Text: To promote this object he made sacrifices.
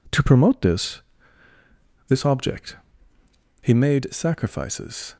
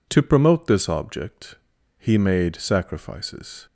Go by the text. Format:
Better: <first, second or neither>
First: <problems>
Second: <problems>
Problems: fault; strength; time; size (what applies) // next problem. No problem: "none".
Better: second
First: says "this" twice; at 2.0 s // pauses between "object" and "he"; noticeable; at 2.7 s; 0.86 s long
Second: pauses between "object" and "he"; at 1.5 s; 0.42 s long